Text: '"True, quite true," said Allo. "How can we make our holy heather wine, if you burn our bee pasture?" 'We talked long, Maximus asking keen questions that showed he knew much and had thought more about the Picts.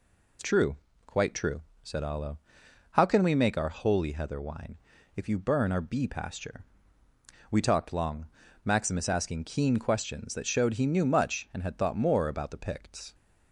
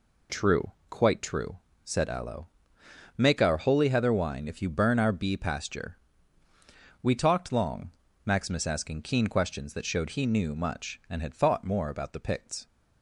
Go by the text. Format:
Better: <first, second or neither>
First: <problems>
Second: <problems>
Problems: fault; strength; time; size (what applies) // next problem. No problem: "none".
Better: first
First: none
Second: skips "How can we"; at 2.8 s